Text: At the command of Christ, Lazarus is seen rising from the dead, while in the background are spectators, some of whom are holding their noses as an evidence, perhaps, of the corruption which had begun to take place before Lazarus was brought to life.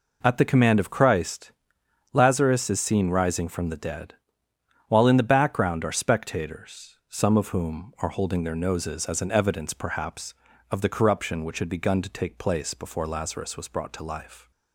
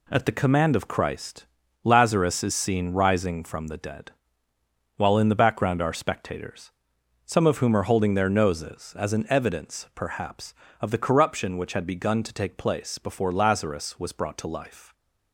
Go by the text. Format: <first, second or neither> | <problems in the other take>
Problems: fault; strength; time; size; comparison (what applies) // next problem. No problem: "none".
neither | none